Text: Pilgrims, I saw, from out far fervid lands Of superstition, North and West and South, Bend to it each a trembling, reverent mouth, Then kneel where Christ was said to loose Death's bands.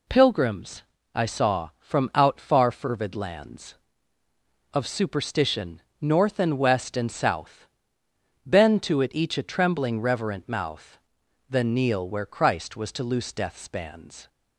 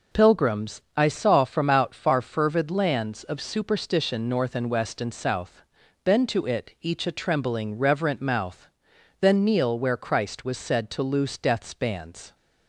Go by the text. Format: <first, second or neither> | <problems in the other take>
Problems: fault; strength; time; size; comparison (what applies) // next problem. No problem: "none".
second | skips "said"; at 12.9 s